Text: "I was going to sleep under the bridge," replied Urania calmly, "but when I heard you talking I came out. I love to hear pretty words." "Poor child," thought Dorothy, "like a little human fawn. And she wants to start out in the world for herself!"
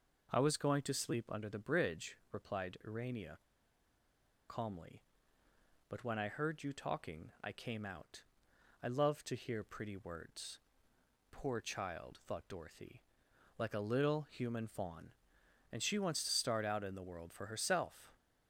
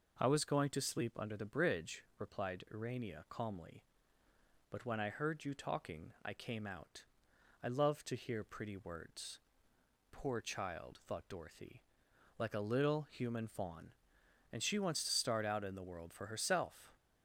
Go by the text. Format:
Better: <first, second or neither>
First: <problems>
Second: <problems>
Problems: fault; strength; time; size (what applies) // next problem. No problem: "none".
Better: second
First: pauses between "Urania" and "calmly"; at 3.3 s; 1.1 s long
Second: none